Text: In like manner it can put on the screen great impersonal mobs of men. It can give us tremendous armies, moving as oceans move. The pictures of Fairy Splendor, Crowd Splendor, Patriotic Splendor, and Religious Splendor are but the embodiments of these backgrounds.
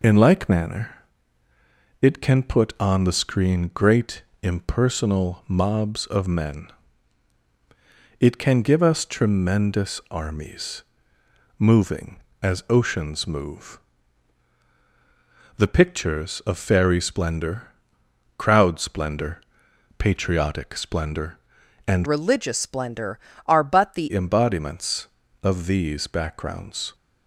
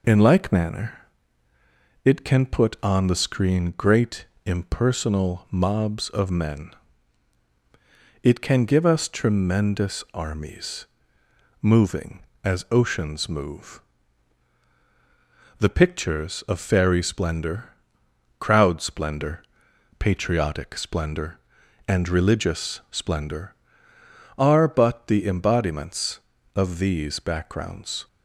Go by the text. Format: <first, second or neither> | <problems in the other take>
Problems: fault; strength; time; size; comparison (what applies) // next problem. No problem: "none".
second | pauses between "manner" and "it"; at 0.9 s; 1.1 s long; also in the second // pauses between "great" and "impersonal"; slight; at 4.2 s; 0.20 s long; slight in the second // changes voice from "Religious" to "the"; from 22.0 to 24.1 s; 2.1 s long